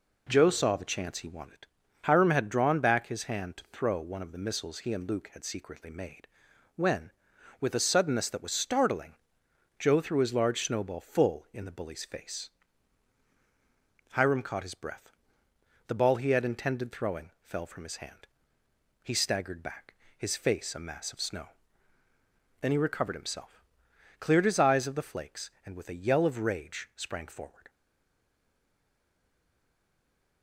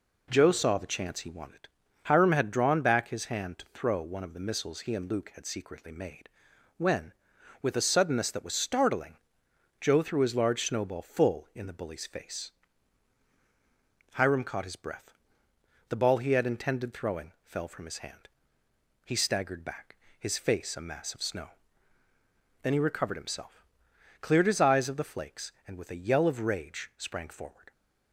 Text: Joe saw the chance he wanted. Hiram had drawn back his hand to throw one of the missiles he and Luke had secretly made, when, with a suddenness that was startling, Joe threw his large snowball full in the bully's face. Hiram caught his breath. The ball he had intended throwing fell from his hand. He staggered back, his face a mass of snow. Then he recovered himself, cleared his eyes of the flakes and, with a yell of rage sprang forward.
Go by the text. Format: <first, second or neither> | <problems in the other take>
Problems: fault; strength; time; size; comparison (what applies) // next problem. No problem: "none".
second | stays silent after the last word; strong; from 27.6 s on; 2.8 s long